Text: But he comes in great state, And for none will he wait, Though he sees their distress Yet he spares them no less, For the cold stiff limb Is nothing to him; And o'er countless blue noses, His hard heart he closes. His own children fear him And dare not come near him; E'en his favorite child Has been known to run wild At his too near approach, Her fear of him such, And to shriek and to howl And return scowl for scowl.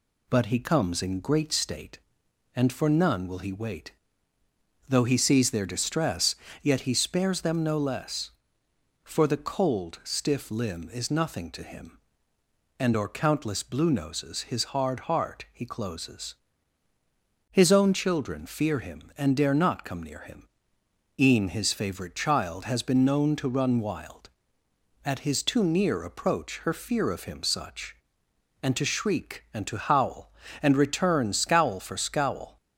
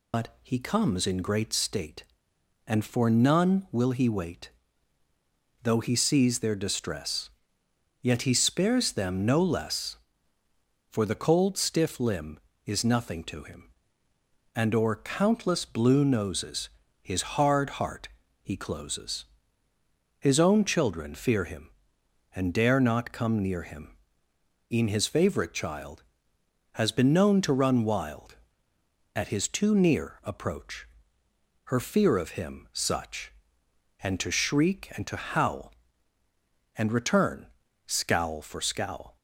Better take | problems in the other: first | loses the start of "But"; at 0.1 s; 95 ms // pauses between "distress" and "Yet"; noticeable; at 7.3 s; 0.72 s long; slight in the first // pauses between "heart" and "he"; slight; at 18.0 s; 0.34 s long // pauses between "return" and "scowl"; at 37.4 s; 0.40 s long

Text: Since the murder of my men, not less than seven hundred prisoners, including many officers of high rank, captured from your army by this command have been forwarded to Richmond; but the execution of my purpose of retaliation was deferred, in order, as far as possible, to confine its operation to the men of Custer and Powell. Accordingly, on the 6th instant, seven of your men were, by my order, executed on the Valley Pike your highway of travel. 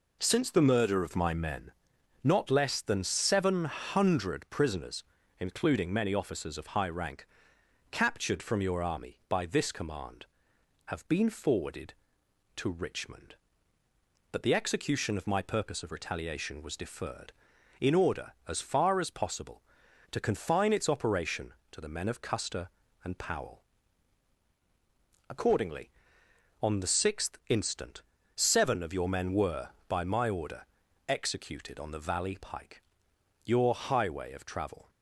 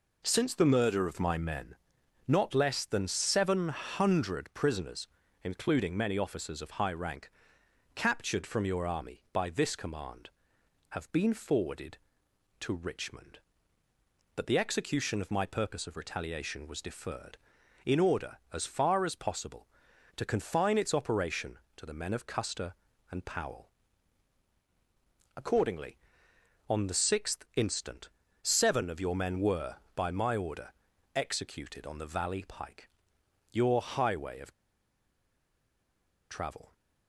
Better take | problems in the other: first | pauses between "Pike" and "your"; noticeable; at 32.8 s; 0.62 s long; noticeable in the first // pauses between "of" and "travel"; strong; at 34.5 s; 1.7 s long

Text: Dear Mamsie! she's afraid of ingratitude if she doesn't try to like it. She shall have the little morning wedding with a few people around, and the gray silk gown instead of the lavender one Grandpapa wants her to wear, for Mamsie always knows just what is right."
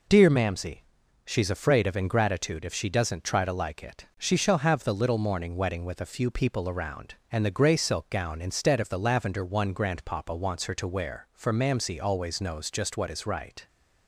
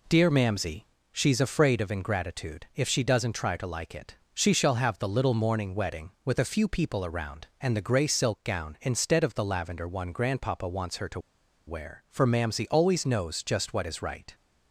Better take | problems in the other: first | pauses between "to" and "wear"; noticeable; at 11.1 s; 0.48 s long

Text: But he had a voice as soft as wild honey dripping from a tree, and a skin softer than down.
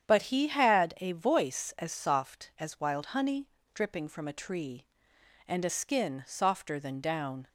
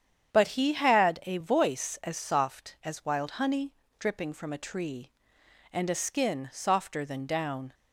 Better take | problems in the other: neither | starts louder than the rest; strong; the same in both // pauses between "honey" and "dripping"; slight; the same in both

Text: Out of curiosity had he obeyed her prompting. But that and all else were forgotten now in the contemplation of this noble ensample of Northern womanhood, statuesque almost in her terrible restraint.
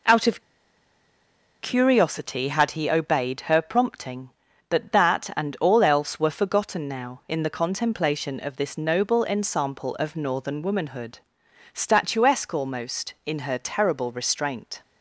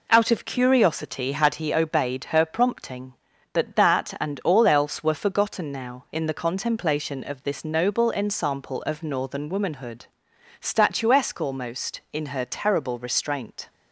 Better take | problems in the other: second | pauses between "of" and "curiosity"; at 0.4 s; 1.2 s long

